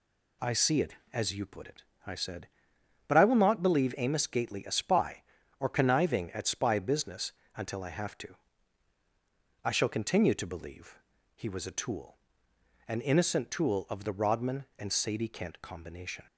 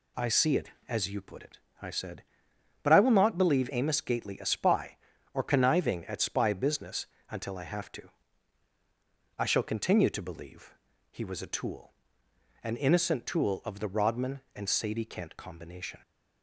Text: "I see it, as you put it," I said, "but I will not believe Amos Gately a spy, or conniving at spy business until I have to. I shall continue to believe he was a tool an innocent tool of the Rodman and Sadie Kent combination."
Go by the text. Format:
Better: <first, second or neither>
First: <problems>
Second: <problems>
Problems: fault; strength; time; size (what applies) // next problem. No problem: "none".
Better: neither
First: pauses between "business" and "until"; slight; at 7.3 s; 0.24 s long // pauses between "believe" and "he"; slight; at 10.9 s; 0.34 s long // pauses between "tool" and "an"; noticeable; at 12.1 s; 0.70 s long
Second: pauses between "business" and "until"; slight; at 7.0 s; 0.24 s long // pauses between "believe" and "he"; slight; at 10.7 s; 0.34 s long // pauses between "tool" and "an"; noticeable; at 11.9 s; 0.70 s long